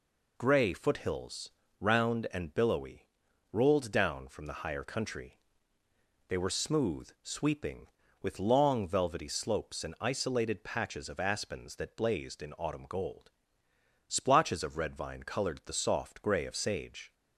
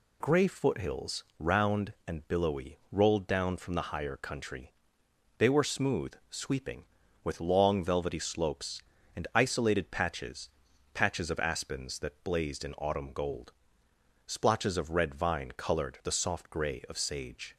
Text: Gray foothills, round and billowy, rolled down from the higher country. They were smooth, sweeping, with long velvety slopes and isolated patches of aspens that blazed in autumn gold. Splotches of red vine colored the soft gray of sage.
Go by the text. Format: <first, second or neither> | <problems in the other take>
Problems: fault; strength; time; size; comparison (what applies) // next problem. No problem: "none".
first | says "patches" twice; at 10.9 s